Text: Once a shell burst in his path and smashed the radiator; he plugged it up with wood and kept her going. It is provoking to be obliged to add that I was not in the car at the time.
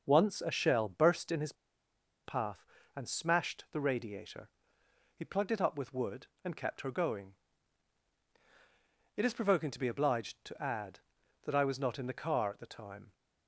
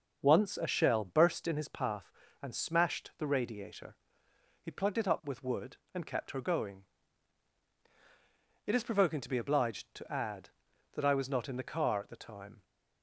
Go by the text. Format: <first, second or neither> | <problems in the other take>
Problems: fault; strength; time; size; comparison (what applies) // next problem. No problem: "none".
second | starts louder than the rest; until 1.0 s; 6 dB; also in the second // pauses between "his" and "path"; noticeable; at 1.5 s; 0.72 s long